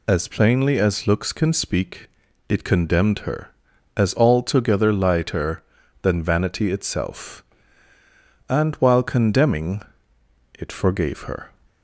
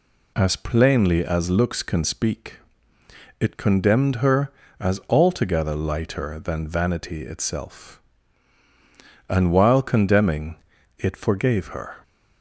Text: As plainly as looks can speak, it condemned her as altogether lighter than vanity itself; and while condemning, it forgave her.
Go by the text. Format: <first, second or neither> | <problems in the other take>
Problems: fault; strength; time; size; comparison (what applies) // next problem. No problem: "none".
neither | none